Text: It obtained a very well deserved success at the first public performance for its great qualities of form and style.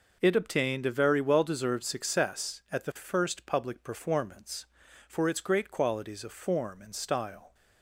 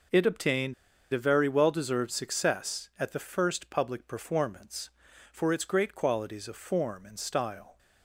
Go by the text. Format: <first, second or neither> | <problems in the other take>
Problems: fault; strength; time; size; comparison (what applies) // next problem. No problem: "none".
first | pauses between "obtained" and "a"; at 0.7 s; 0.39 s long